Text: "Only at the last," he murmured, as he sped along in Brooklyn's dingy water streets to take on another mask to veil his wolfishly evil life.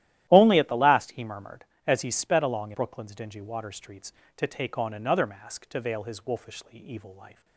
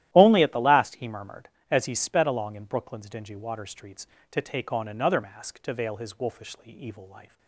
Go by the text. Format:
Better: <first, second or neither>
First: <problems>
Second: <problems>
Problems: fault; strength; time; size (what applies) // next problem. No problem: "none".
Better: second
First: starts louder than the rest; strong; until 1.3 s; 13 dB // skips "in"; at 2.7 s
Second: starts louder than the rest; strong; until 1.1 s; 13.5 dB